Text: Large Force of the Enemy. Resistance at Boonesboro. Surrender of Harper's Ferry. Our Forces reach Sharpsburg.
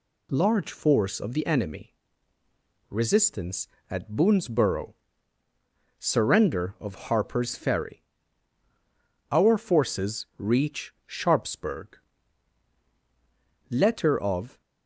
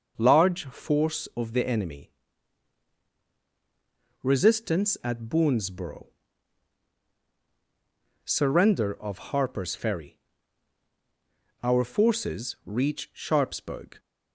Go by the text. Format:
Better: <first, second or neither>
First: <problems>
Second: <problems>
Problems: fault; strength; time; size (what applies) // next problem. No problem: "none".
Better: second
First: pauses between "reach" and "Sharpsburg"; slight; at 10.9 s; 0.16 s long // goes on to say "Letter of"; noticeable; from 13.7 s on; 0.90 s long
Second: none